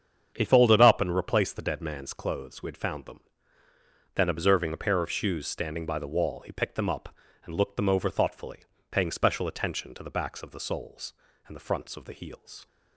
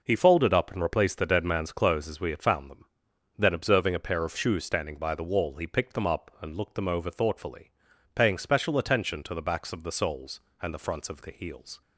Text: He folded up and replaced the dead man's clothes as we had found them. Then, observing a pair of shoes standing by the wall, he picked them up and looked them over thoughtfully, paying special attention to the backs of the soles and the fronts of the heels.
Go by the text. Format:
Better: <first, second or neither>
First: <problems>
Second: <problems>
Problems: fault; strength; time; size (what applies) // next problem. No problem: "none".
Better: second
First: starts louder than the rest; strong; until 1.3 s; 7.5 dB // skips "as"; at 2.6 s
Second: none